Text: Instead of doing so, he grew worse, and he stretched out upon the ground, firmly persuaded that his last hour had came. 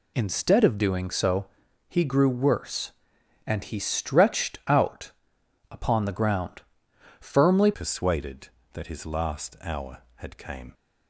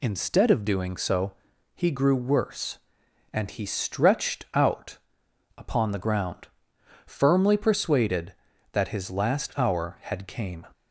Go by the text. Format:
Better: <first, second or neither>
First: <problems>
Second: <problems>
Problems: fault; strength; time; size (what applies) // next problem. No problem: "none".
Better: second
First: pauses between "out" and "upon"; noticeable; at 5.0 s; 0.62 s long // changes voice at "persuaded"; from 7.7 s on; 3.0 s long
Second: pauses between "out" and "upon"; noticeable; at 4.9 s; 0.62 s long